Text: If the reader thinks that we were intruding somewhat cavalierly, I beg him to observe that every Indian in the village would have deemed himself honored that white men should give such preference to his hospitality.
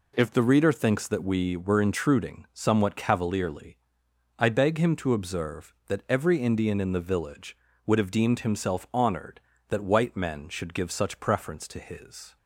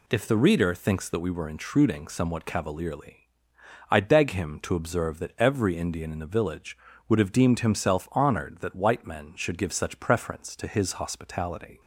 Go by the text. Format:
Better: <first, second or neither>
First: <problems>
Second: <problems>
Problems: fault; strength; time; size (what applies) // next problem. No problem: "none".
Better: second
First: stops before "hospitality"; at 12.3 s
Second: none